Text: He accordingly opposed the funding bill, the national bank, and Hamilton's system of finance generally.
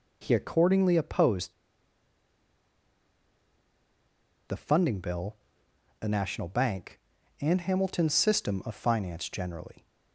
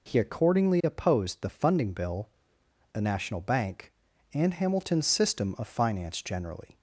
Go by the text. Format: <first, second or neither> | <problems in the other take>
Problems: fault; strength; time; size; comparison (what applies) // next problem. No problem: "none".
second | pauses between "opposed" and "the"; strong; at 1.5 s; 2.9 s long